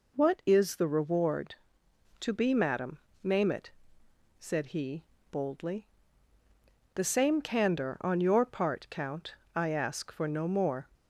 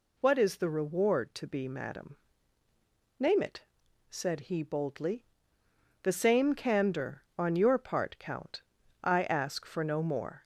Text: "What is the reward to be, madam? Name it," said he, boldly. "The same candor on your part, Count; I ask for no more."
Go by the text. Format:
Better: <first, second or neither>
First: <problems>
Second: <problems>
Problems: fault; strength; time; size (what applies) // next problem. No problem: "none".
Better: neither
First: none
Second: none